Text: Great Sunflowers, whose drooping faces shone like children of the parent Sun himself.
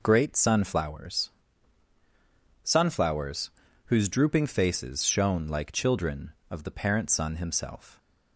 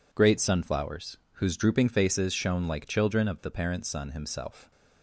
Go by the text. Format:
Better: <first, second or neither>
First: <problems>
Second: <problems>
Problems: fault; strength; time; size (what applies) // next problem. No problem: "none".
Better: second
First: says "Sunflowers" twice; at 2.6 s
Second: none